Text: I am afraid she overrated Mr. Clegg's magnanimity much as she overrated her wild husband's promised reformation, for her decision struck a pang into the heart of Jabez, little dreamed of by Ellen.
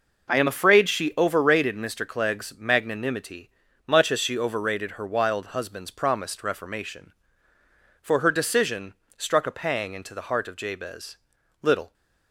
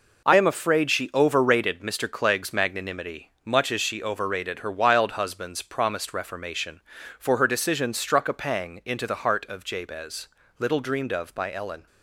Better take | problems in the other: second | pauses between "magnanimity" and "much"; at 3.4 s; 0.40 s long // pauses between "decision" and "struck"; slight; at 8.9 s; 0.24 s long // stops before "dreamed of by Ellen"; at 11.9 s

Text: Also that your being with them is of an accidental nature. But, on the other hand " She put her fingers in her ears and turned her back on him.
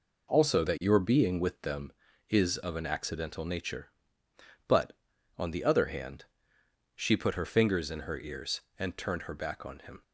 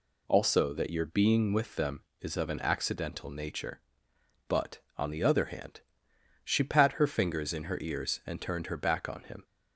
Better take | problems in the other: first | says "pat" for "put"; at 6.6 s

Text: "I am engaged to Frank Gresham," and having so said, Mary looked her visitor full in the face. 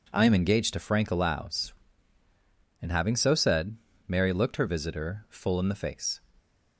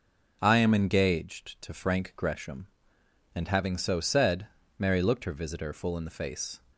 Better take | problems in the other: second | says "Allows" for "Gresham"; at 1.1 s

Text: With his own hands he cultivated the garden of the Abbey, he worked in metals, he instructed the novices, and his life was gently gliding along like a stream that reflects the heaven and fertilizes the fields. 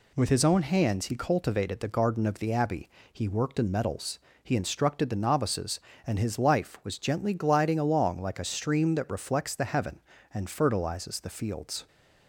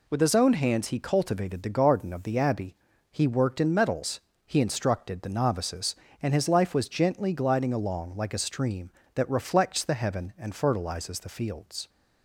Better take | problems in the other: neither | none

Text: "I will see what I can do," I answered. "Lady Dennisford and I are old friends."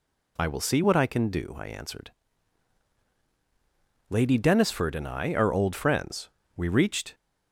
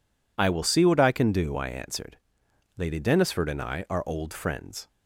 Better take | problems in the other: second | goes on to say "We reached"; from 6.5 s on; 0.58 s long

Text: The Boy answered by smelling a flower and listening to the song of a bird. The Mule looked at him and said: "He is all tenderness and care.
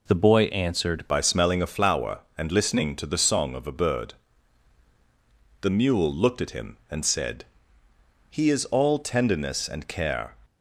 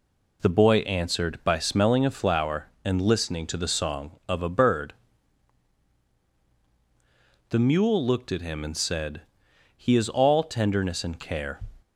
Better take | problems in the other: second | changes voice at "by"; from 1.0 s on; 9.3 s long

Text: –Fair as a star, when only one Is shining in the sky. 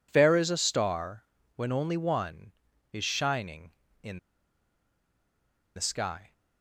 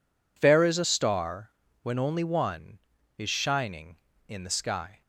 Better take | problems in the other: second | pauses between "in" and "the"; strong; at 4.1 s; 1.5 s long

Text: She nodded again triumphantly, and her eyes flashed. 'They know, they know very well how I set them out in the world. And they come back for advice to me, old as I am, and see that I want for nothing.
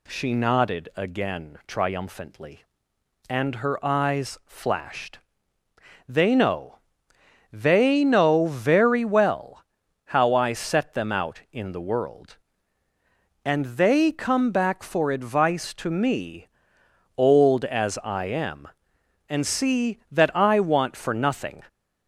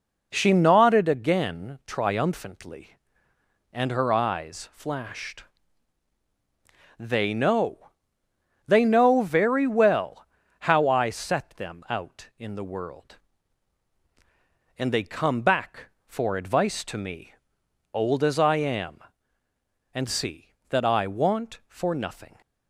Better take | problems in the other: neither | pauses between "well" and "how"; the same in both

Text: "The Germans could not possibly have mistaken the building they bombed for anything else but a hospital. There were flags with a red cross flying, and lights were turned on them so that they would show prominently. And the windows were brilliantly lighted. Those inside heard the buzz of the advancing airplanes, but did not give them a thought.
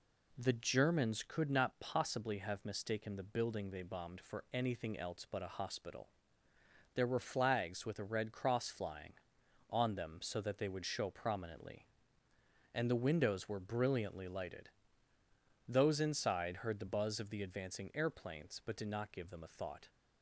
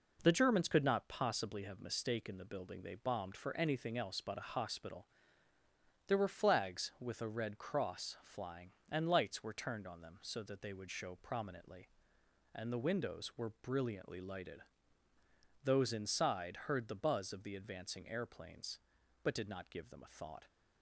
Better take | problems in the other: second | skips "and lights were turned"; at 9.4 s

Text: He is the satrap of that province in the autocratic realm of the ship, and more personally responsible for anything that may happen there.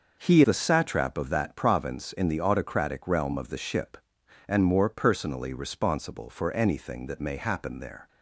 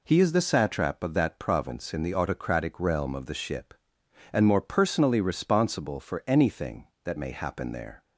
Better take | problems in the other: second | skips "is"; at 0.4 s

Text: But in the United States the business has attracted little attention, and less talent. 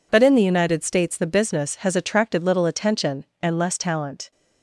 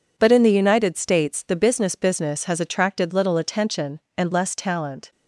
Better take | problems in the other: first | says "business" twice; at 1.9 s

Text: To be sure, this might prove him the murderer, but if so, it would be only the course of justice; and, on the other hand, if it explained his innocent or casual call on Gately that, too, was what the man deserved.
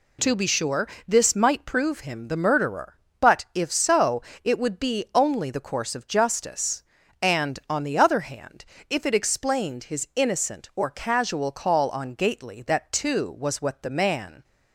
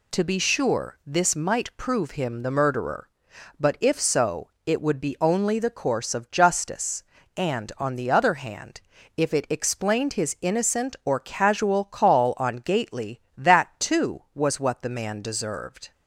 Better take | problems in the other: second | stops before "deserved"; at 14.4 s

